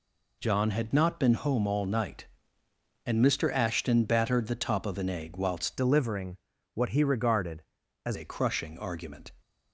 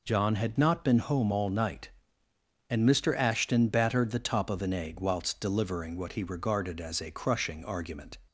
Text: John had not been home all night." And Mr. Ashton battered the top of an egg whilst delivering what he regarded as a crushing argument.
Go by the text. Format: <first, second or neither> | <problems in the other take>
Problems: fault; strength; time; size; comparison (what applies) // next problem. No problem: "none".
second | changes voice from "delivering" to "as"; from 5.7 to 8.1 s; 2.4 s long // pauses between "delivering" and "what"; slight; at 6.3 s; 0.36 s long